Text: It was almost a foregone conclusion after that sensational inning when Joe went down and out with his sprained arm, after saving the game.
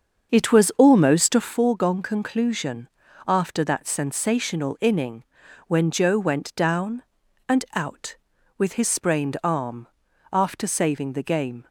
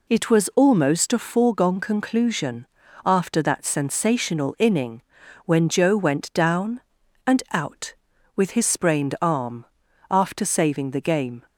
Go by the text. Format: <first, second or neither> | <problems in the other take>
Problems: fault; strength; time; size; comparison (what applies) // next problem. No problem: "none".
second | starts louder than the rest; until 1.6 s; 7 dB // pauses between "conclusion" and "after"; at 2.8 s; 0.38 s long; also in the second // pauses between "inning" and "when"; at 5.2 s; 0.42 s long; also in the second